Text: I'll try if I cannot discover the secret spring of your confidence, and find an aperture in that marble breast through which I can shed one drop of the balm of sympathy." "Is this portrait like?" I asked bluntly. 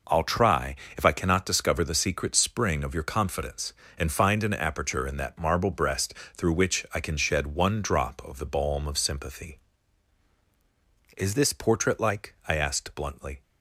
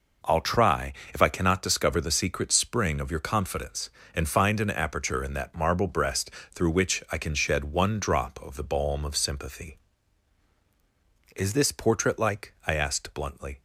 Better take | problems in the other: neither | pauses between "try" and "if"; slight; the same in both // pauses between "breast" and "through"; slight; the same in both

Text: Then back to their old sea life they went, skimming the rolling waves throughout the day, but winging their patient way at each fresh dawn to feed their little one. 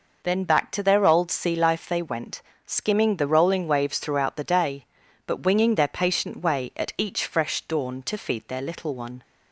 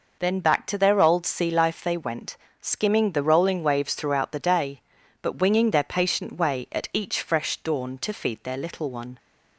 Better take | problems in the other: neither | none

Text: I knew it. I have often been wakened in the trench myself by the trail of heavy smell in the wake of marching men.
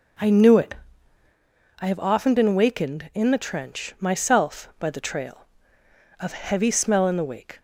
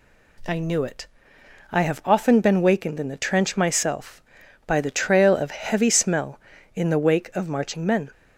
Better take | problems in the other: second | stops before "of marching men"; at 7.5 s

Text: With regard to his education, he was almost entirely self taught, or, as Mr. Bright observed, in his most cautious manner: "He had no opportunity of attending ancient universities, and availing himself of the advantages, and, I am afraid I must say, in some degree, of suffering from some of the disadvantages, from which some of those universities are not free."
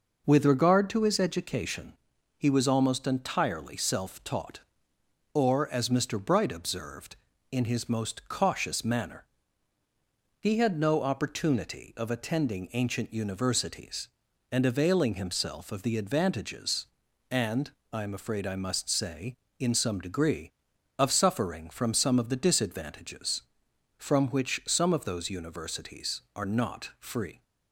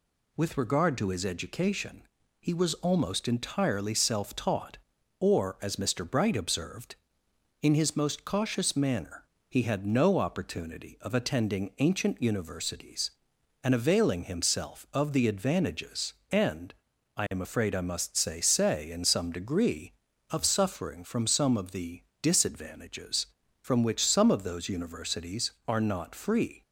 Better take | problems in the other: first | says "say" twice; at 18.4 s // pauses between "the" and "disadvantages"; slight; at 22.0 s; 0.18 s long

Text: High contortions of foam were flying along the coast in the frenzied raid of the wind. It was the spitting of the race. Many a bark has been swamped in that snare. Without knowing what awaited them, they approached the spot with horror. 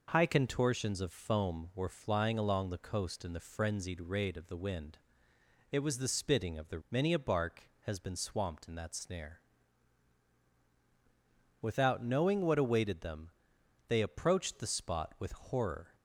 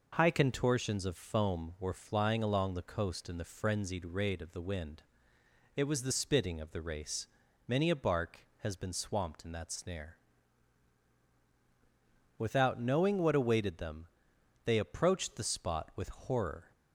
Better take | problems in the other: second | skips "race"; at 6.8 s

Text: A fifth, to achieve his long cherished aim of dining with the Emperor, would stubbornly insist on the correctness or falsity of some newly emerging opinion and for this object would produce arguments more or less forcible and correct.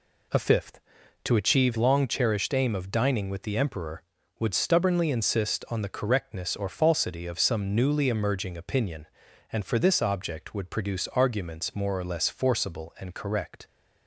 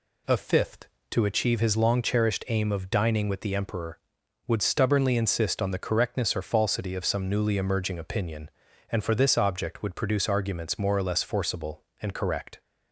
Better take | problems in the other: second | skips "his"; at 1.7 s

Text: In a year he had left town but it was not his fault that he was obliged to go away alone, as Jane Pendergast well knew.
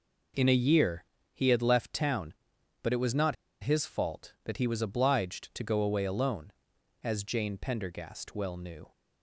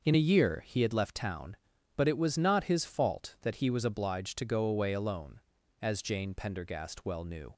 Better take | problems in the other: second | pauses between "year" and "he"; slight; at 1.0 s; 0.28 s long // pauses between "not" and "his"; slight; at 3.3 s; 0.27 s long

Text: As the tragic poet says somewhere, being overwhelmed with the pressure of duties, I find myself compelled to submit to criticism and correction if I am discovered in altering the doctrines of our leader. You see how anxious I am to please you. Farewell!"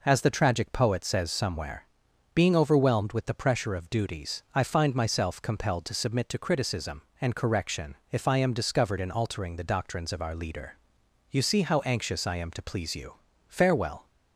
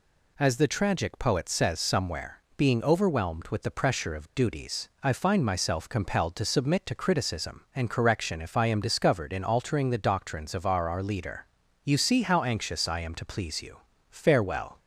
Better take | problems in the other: first | says "our" twice; at 10.8 s

